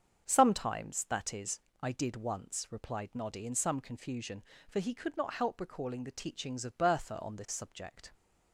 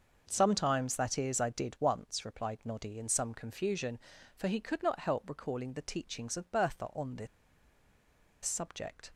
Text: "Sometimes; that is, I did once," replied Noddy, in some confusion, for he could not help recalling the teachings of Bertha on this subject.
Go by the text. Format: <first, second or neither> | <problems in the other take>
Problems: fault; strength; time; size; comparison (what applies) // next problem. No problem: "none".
first | starts louder than the rest; until 1.2 s; 6 dB; strong in the first // pauses between "this" and "subject"; at 7.2 s; 1.1 s long